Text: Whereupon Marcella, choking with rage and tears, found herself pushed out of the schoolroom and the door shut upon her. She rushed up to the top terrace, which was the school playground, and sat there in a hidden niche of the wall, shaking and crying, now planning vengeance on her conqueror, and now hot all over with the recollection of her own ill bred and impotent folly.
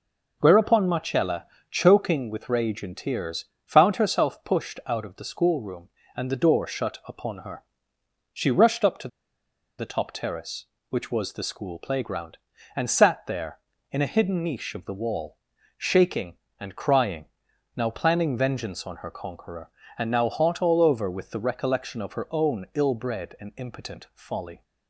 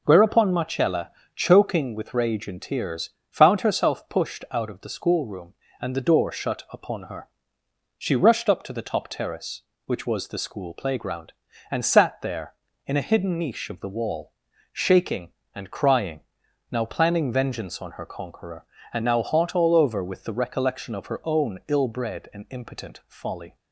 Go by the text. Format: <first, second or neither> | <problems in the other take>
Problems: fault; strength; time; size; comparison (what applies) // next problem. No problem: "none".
second | pauses between "to" and "the"; noticeable; at 9.0 s; 0.70 s long